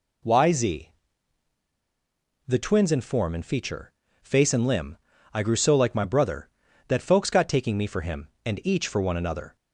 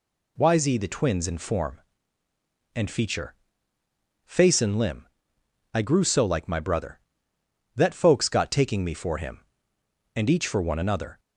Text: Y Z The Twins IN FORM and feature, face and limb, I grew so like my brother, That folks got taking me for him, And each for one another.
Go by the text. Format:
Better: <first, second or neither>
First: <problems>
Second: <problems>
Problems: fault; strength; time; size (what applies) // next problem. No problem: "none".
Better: second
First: pauses between "Z" and "The"; strong; at 0.8 s; 1.5 s long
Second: none